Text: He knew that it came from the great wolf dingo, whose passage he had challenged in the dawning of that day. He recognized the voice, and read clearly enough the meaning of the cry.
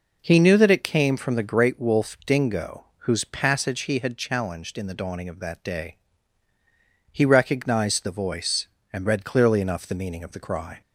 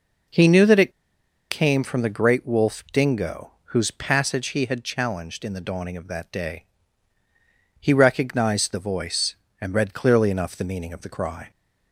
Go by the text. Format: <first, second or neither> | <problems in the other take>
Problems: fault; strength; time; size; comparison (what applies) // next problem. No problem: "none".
first | pauses between "it" and "came"; noticeable; at 0.9 s; 0.58 s long